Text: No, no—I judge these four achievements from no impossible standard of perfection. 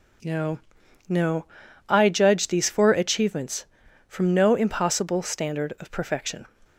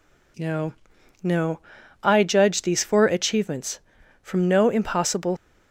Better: first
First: none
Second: stops before "standard of perfection"; at 5.3 s

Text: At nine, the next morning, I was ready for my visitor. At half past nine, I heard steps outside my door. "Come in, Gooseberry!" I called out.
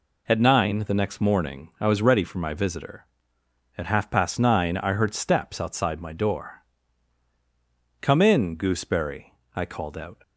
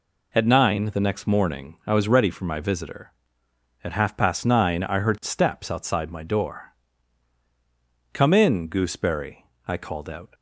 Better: neither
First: none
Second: none

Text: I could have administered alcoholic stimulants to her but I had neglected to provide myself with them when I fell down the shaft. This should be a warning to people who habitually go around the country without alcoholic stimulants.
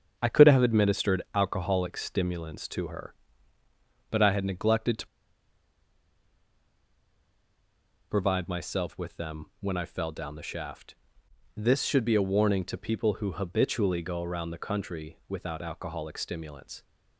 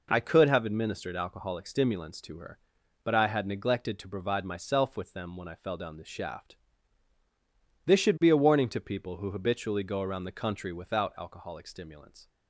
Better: second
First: starts louder than the rest; strong; until 1.1 s; 7.5 dB // pauses between "to" and "provide"; strong; at 5.0 s; 3.0 s long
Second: none

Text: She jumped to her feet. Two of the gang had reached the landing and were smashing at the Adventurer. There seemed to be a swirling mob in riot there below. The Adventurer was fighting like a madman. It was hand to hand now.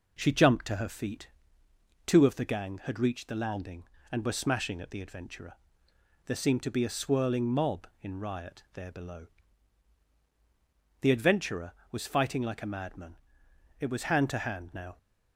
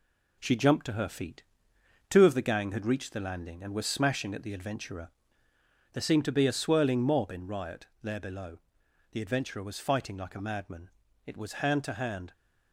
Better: first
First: none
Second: pauses between "riot" and "there"; slight; at 7.8 s; 0.16 s long // stops before "now"; at 12.3 s

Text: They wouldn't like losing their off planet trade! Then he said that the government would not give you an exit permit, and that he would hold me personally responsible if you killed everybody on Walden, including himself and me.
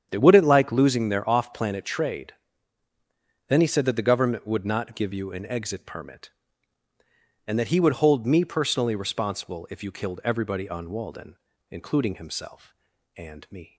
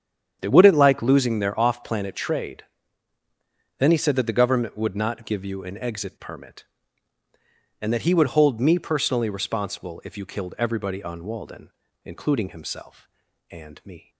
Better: neither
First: starts louder than the rest; strong; until 1.1 s; 8.5 dB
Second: starts louder than the rest; strong; until 1.4 s; 8.5 dB

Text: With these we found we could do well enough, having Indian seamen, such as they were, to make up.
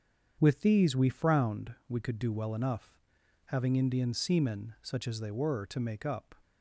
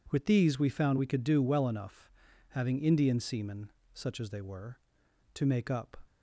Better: second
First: starts louder than the rest; strong; until 1.4 s; 7.5 dB // says "frowned" for "found"; at 1.1 s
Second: none

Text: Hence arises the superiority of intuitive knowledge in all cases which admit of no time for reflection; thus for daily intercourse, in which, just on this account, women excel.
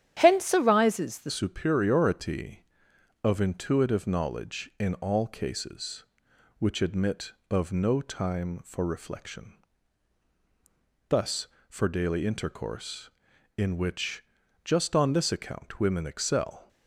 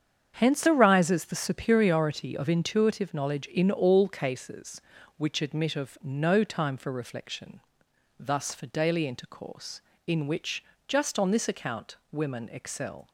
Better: second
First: starts louder than the rest; strong; until 1.1 s; 10.5 dB // changes voice at "superiority"; from 1.2 s on; 15.4 s long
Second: starts louder than the rest; strong; until 1.3 s; 7.5 dB

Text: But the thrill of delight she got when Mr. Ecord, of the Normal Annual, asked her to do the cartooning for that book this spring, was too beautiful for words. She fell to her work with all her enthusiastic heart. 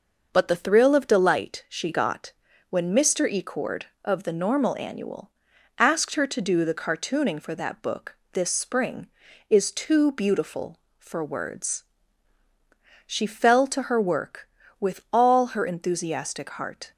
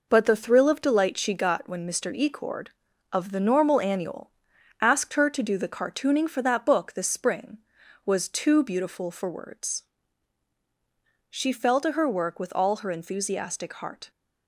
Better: second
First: pauses between "got" and "when"; at 2.3 s; 0.38 s long // pauses between "book" and "this"; slight; at 8.1 s; 0.20 s long // says "is" for "was"; at 9.4 s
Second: none

